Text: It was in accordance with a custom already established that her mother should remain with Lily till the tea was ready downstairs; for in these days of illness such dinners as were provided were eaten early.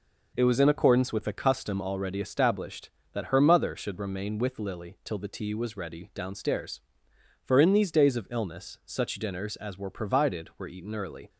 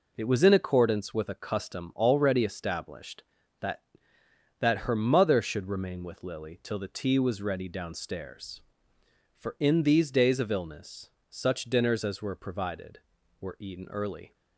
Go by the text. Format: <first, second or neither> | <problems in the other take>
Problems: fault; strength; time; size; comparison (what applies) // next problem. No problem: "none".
first | says "that" twice; at 4.5 s // pauses between "illness" and "such"; slight; at 11.0 s; 0.22 s long